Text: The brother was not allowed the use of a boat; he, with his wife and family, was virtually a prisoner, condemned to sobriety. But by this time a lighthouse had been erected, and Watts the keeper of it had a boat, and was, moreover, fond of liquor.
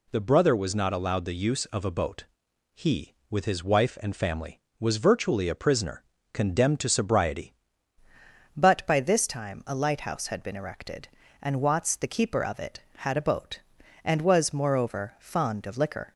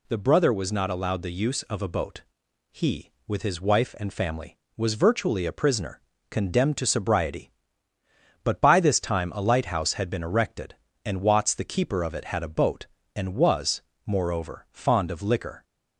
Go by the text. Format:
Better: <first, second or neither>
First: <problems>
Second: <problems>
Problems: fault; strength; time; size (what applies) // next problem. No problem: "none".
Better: second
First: changes voice at "But"; from 8.5 s on; 7.6 s long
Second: none